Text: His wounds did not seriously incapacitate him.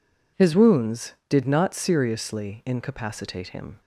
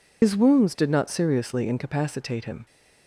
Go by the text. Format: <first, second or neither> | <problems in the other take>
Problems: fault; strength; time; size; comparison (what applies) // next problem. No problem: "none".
first | loses the start of "His"; at 0.2 s; 60 ms